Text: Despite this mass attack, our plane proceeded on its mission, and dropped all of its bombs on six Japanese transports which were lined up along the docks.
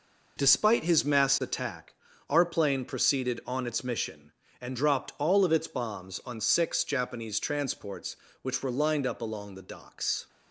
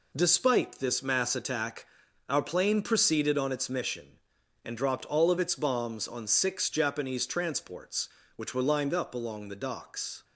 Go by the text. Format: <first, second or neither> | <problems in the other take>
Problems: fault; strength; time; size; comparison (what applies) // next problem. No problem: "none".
second | says "his" for "this"; at 0.8 s